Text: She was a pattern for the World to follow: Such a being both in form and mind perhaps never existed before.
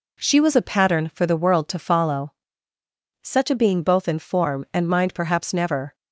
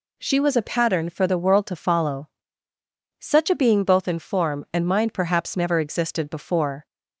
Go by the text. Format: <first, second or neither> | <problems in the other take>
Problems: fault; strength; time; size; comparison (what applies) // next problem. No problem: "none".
second | stops before "existed before"; at 5.9 s